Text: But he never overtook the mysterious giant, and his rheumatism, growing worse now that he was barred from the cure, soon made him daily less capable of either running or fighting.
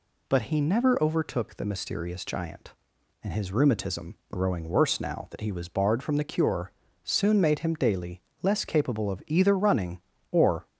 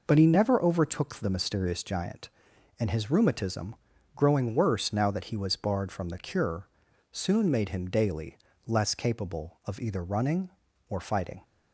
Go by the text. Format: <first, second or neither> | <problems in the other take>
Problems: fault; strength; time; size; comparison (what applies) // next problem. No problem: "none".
second | pauses between "daily" and "less"; slight; at 8.2 s; 0.22 s long; slight in the second // stops before "fighting"; at 10.6 s